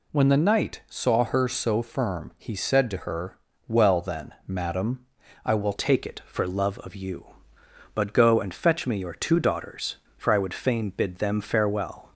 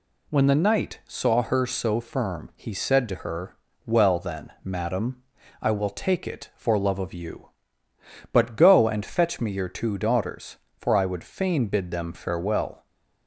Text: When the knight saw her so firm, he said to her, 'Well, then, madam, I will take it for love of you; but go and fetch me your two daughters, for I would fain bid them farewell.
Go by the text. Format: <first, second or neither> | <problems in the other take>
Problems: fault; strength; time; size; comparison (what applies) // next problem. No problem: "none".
second | changes voice at "take"; from 5.7 s on; 6.4 s long